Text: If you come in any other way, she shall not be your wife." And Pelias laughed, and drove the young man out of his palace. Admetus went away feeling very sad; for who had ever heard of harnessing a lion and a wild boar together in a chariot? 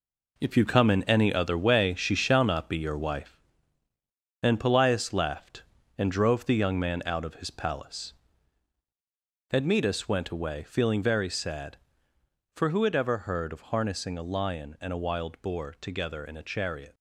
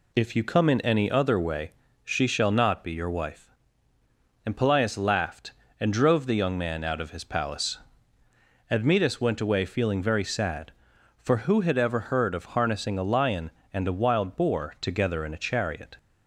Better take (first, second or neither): second